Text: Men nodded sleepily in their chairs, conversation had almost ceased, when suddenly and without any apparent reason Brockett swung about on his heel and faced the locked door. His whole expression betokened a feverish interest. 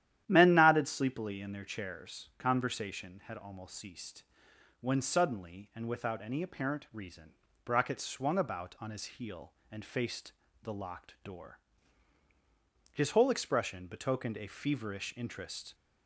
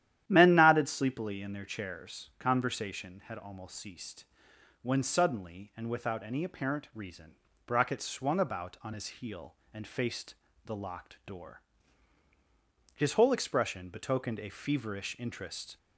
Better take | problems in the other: neither | starts louder than the rest; strong; the same in both // pauses between "reason" and "Brockett"; slight; the same in both // pauses between "faced" and "the"; slight; the same in both

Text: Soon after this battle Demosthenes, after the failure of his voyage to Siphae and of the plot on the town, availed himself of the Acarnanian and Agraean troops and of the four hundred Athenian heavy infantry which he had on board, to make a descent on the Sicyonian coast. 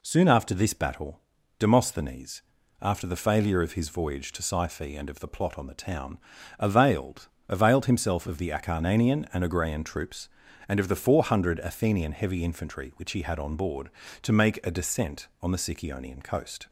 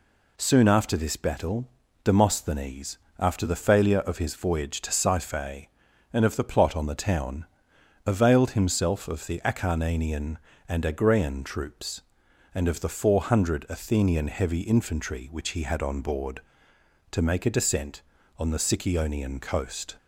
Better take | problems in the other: second | pauses between "battle" and "Demosthenes"; at 1.2 s; 0.38 s long; slight in the second // says "availed" twice; at 7.4 s

